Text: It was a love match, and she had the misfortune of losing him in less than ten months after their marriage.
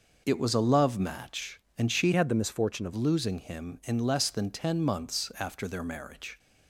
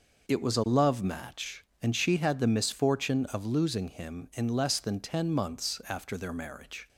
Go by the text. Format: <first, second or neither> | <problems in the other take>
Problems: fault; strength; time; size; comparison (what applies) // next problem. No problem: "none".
second | changes voice from "had" to "of"; from 2.1 to 2.9 s; 0.8 s long